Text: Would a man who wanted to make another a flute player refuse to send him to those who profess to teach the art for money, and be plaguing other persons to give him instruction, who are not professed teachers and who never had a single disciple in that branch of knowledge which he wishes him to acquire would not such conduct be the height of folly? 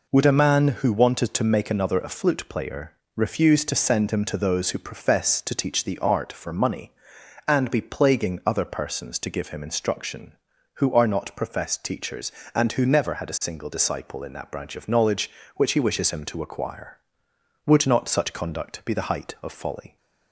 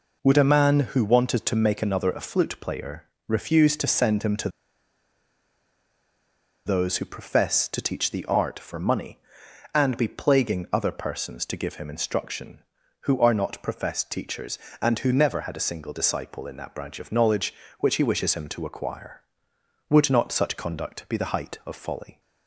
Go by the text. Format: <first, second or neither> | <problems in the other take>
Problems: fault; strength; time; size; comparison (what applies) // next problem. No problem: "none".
first | pauses between "player" and "refuse"; slight; at 3.0 s; 0.24 s long; slight in the first // pauses between "to" and "those"; strong; at 4.4 s; 2.1 s long